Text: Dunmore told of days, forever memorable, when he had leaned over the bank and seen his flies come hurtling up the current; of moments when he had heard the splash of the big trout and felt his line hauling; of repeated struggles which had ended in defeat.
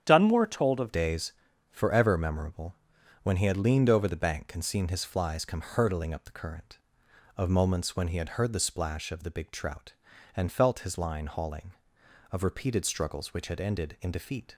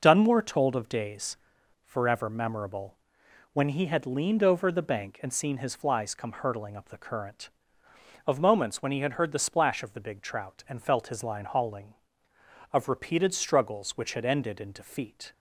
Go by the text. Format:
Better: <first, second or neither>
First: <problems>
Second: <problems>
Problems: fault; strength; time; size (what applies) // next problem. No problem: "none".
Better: second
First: starts louder than the rest; strong; until 1.0 s; 9 dB // changes voice at "days"; from 0.9 s on; 13.6 s long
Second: none